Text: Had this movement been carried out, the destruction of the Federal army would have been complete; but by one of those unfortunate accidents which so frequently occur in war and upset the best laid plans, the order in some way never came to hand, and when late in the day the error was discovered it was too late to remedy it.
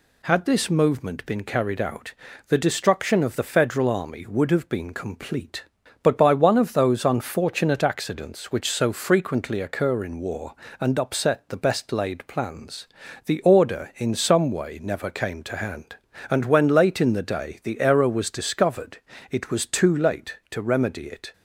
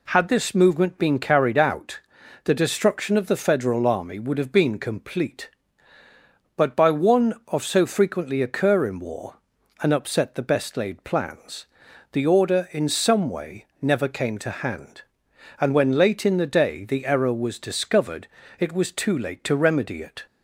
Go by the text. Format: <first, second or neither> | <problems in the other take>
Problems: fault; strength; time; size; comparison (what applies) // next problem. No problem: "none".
first | skips "those unfortunate accidents which"; at 7.6 s // pauses between "way" and "never"; slight; at 13.6 s; 0.16 s long // pauses between "discovered" and "it"; slight; at 18.2 s; 0.32 s long; slight in the first